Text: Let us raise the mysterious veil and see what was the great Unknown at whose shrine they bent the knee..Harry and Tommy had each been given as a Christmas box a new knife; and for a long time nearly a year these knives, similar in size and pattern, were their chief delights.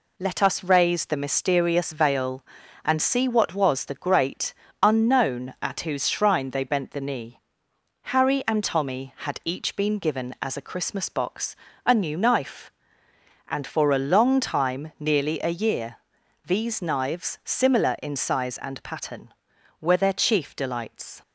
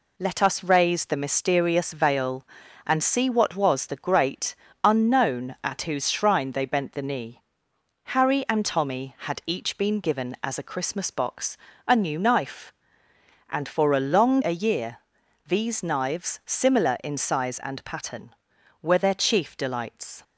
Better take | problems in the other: first | pauses between "great" and "Unknown"; slight; at 4.5 s; 0.30 s long; slight in the first // pauses between "box" and "a"; slight; at 11.5 s; 0.30 s long; slight in the first // skips "time nearly"; at 14.4 s // pauses between "year" and "these"; noticeable; at 14.9 s; 0.50 s long; noticeable in the first

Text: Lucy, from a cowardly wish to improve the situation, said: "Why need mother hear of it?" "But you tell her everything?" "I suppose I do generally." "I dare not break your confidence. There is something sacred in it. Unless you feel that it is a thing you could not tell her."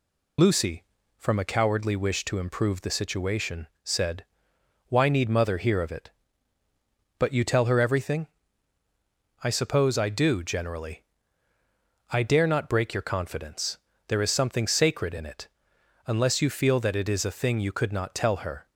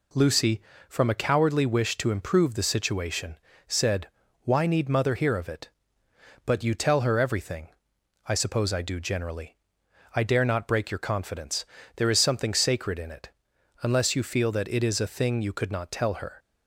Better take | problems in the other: second | loses the start of "Lucy"; at 0.3 s; 55 ms

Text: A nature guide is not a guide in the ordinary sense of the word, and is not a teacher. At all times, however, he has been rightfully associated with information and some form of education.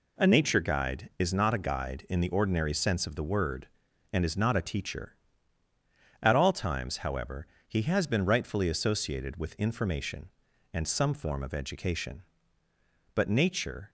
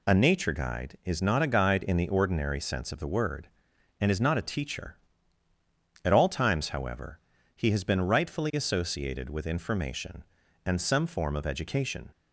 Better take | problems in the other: second | goes on to say "But nature"; noticeable; from 13.1 s on; 0.76 s long

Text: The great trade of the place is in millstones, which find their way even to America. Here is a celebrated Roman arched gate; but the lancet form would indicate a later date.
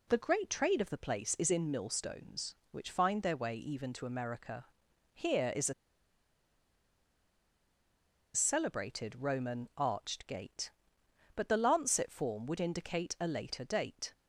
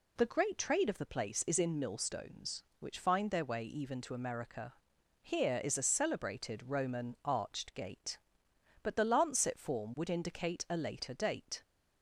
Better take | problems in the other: second | pauses between "a" and "celebrated"; strong; at 5.7 s; 2.6 s long

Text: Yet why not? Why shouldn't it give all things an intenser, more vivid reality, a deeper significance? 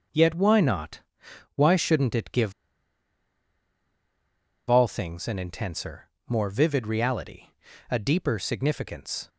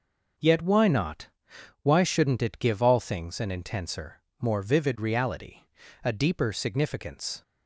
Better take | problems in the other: second | pauses between "give" and "all"; strong; at 2.5 s; 2.1 s long

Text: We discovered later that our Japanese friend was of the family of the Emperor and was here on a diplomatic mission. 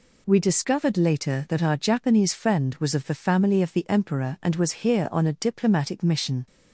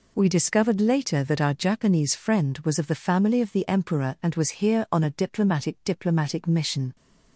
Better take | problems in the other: first | says "diplomatic" twice; at 5.8 s

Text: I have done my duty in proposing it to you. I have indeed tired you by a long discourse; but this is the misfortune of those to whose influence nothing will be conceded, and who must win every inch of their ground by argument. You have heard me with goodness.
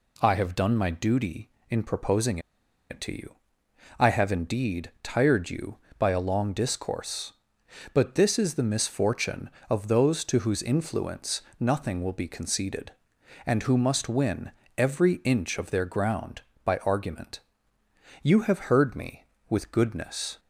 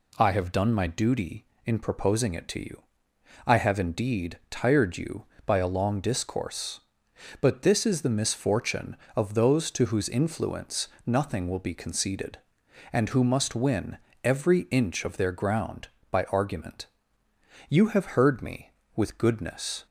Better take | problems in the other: second | pauses between "proposing" and "it"; noticeable; at 2.3 s; 0.51 s long // pauses between "influence" and "nothing"; slight; at 11.4 s; 0.18 s long; slight in the second // pauses between "win" and "every"; slight; at 14.4 s; 0.26 s long; slight in the second

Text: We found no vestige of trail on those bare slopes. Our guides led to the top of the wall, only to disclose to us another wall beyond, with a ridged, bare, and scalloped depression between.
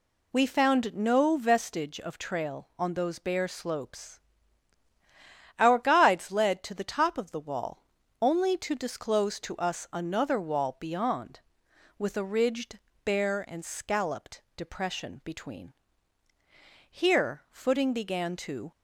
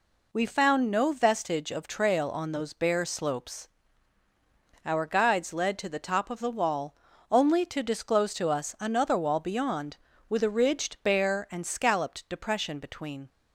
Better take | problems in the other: second | goes on to say "Here footing began to"; strong; from 16.9 s on; 1.7 s long

